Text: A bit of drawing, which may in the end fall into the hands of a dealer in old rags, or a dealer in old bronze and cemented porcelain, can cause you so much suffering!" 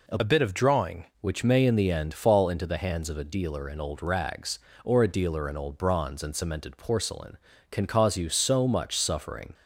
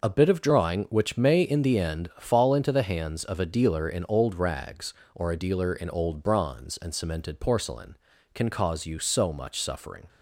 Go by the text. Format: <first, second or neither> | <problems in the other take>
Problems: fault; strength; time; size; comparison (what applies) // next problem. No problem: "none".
second | changes voice from "bit" to "drawing"; from 0.2 to 1.0 s; 0.8 s long